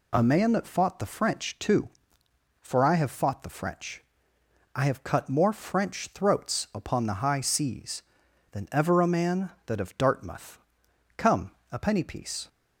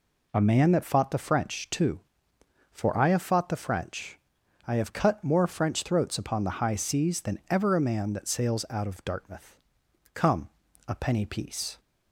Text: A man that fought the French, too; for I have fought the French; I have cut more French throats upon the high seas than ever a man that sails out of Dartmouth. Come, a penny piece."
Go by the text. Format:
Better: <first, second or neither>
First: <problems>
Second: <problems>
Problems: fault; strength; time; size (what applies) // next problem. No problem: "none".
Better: second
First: skips "sails out"; at 9.7 s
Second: none